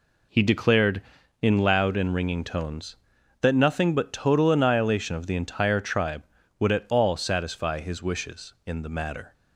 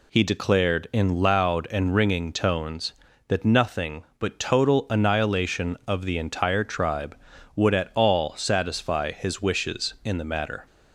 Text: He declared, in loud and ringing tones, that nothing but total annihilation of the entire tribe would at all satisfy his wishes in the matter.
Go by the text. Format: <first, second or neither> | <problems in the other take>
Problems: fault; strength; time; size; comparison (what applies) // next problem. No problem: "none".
neither | none